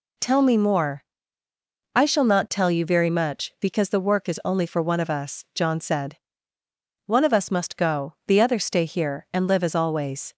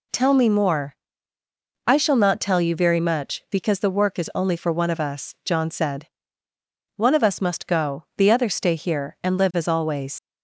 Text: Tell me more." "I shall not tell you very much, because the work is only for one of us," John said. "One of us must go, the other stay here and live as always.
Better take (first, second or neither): first